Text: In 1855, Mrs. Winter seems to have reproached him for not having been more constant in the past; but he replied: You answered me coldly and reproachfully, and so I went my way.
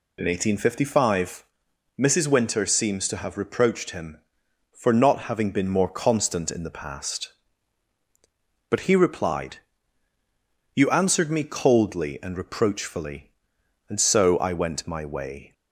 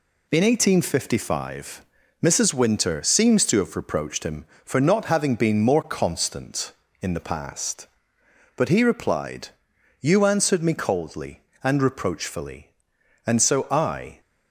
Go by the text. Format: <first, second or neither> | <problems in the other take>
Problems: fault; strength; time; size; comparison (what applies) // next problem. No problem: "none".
first | stops before "went my way"; at 14.2 s